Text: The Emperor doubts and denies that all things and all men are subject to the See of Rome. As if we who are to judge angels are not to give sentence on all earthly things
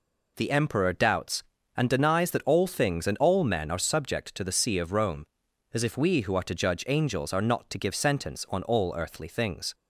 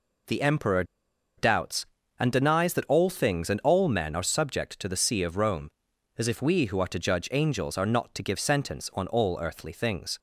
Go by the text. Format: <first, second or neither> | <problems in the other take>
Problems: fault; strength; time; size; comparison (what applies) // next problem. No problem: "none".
first | pauses between "Emperor" and "doubts"; noticeable; at 0.8 s; 0.54 s long